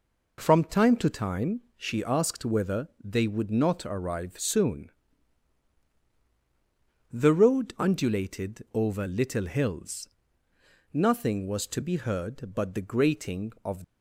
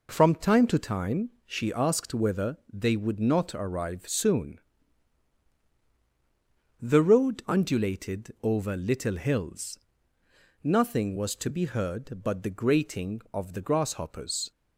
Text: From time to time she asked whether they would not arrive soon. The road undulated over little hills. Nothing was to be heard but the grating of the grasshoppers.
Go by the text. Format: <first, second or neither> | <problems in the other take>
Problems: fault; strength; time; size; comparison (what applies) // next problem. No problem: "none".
second | pauses between "whether" and "they"; slight; at 2.8 s; 0.16 s long; slight in the second // stops before "the grasshoppers"; at 13.8 s